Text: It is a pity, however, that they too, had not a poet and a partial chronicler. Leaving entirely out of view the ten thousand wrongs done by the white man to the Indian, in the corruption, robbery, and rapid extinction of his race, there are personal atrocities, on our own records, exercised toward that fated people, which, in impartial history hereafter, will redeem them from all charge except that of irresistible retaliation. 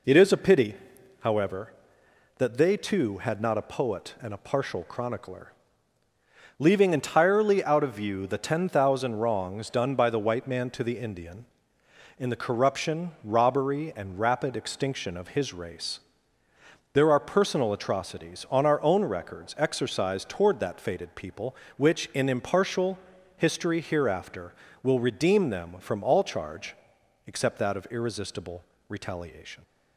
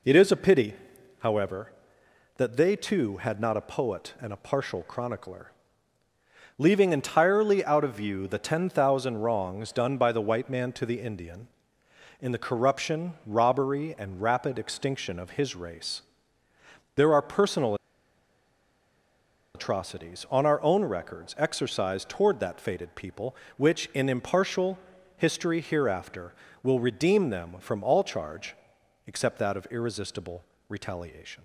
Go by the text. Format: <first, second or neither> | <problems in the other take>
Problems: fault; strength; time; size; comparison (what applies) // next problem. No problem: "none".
first | pauses between "personal" and "atrocities"; strong; at 17.7 s; 1.8 s long // pauses between "impartial" and "history"; at 24.7 s; 0.38 s long; also in the first // pauses between "charge" and "except"; noticeable; at 28.5 s; 0.50 s long; noticeable in the first // pauses between "irresistible" and "retaliation"; slight; at 30.4 s; 0.24 s long; slight in the first